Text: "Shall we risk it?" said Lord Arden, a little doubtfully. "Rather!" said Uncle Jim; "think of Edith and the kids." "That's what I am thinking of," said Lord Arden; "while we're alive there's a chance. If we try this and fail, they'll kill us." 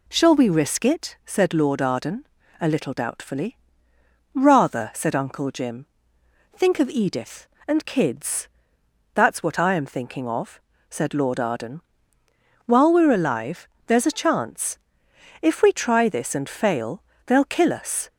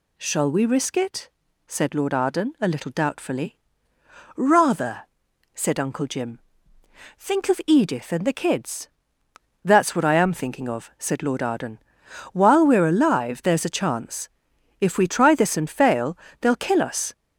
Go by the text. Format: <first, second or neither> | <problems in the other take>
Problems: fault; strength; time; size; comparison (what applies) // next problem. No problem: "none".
second | skips "the"; at 7.8 s // pauses between "alive" and "there's"; slight; at 13.6 s; 0.20 s long